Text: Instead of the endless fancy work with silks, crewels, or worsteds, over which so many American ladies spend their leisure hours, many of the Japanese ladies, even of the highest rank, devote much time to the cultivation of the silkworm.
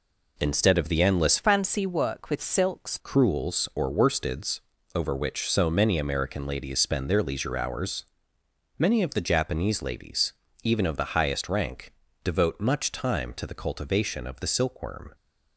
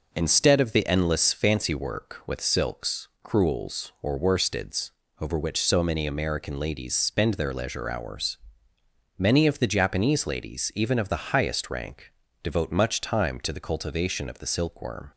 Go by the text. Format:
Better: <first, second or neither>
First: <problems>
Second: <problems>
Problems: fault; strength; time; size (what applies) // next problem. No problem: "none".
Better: second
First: changes voice from "fancy" to "silks"; from 1.3 to 2.9 s; 1.6 s long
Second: none